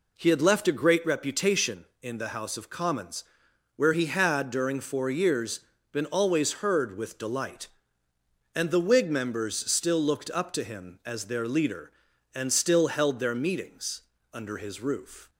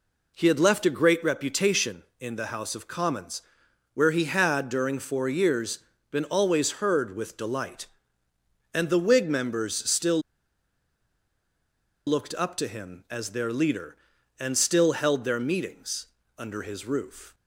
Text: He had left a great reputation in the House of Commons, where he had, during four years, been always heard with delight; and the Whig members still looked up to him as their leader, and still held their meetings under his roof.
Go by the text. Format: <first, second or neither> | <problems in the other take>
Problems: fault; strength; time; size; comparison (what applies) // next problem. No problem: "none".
first | pauses between "still" and "looked"; strong; at 10.1 s; 1.8 s long // pauses between "meetings" and "under"; slight; at 16.0 s; 0.30 s long; slight in the first